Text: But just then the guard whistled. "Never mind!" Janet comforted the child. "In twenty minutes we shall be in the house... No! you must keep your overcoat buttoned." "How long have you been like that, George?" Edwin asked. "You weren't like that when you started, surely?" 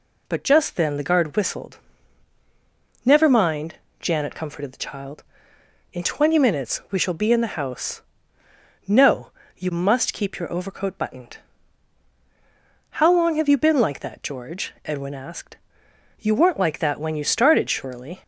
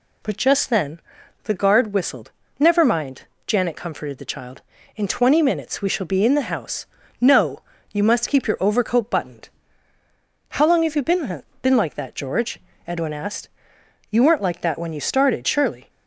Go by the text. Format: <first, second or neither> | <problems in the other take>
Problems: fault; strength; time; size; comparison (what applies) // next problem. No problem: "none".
first | pauses between "then" and "the"; at 1.0 s; 0.42 s long // says "been" twice; at 11.6 s